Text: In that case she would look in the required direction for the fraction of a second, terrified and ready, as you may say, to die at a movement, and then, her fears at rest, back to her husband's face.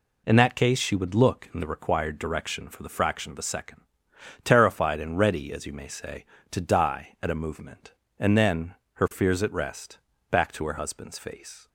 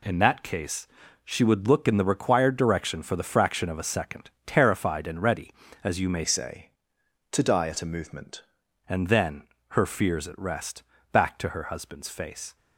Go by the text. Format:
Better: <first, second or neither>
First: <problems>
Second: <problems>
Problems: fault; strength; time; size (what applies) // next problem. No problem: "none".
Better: first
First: none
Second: pauses between "case" and "she"; at 0.8 s; 0.38 s long // changes voice from "say" to "movement"; from 6.2 to 8.4 s; 2.2 s long